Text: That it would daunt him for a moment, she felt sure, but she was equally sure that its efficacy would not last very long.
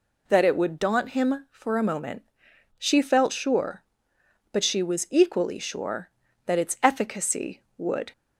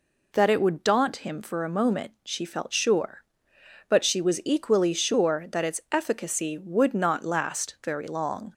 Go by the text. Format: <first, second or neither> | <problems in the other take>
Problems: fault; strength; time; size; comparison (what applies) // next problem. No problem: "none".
second | stops before "not last very long"; at 8.1 s